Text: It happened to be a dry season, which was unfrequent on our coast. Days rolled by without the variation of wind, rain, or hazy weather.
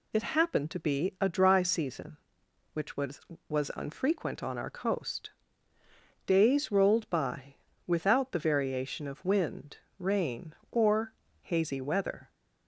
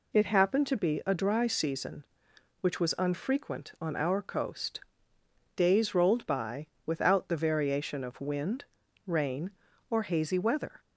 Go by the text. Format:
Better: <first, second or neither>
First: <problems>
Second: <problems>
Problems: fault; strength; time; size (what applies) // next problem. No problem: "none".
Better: second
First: says "was" twice; at 3.4 s // pauses between "by" and "without"; slight; at 7.5 s; 0.30 s long // pauses between "or" and "hazy"; slight; at 11.1 s; 0.30 s long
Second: pauses between "by" and "without"; slight; at 6.6 s; 0.20 s long